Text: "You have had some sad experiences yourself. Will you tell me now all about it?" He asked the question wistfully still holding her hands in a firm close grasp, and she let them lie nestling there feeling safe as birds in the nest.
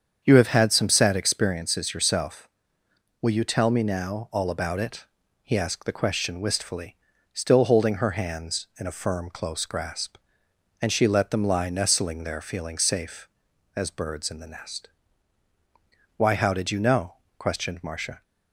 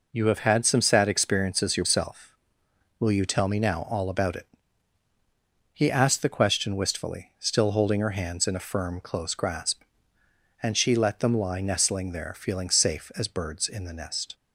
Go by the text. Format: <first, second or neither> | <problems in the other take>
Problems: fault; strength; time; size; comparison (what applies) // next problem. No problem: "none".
second | starts louder than the rest; strong; until 1.2 s; 7 dB // pauses between "wistfully" and "still"; at 6.9 s; 0.38 s long // goes on to say "Why how did you know questioned Marcia"; strong; from 16.1 s on; 2.0 s long